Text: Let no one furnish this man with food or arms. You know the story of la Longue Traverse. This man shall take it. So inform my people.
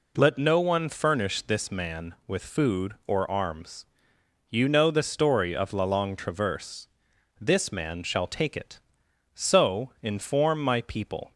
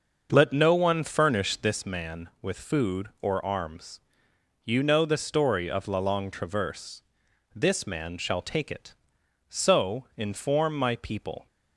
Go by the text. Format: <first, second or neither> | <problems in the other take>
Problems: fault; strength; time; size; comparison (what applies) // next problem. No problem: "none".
first | starts louder than the rest; until 1.9 s; 6.5 dB